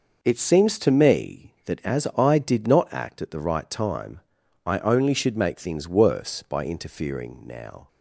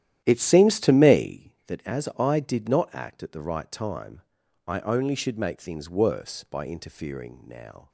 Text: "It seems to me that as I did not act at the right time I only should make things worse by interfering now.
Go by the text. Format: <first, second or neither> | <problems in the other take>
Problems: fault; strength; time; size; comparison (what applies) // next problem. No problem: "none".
first | starts louder than the rest; strong; until 1.5 s; 11.5 dB // pauses between "time" and "I"; noticeable; at 4.2 s; 0.48 s long; noticeable in the first